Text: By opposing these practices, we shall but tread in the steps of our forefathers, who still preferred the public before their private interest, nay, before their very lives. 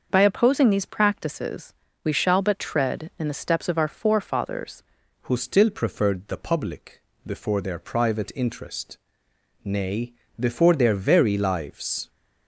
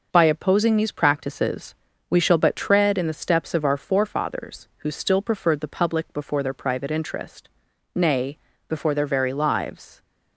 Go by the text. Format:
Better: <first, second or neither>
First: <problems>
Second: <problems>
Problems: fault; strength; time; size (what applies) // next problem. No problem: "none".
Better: second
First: starts louder than the rest; until 1.1 s; 6 dB // changes voice at "who"; from 5.2 s on; 6.8 s long // pauses between "public" and "before"; slight; at 7.0 s; 0.24 s long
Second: none